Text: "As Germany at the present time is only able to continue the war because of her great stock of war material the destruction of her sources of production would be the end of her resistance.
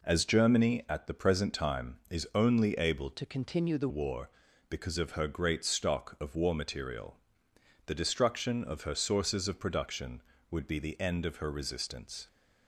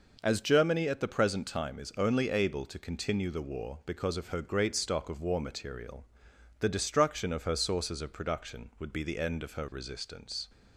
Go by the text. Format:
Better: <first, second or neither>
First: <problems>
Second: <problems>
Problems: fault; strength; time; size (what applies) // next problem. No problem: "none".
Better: second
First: changes voice from "to" to "the"; from 3.1 to 3.8 s; 0.7 s long // pauses between "material" and "the"; noticeable; at 7.1 s; 0.68 s long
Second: pauses between "material" and "the"; noticeable; at 6.0 s; 0.54 s long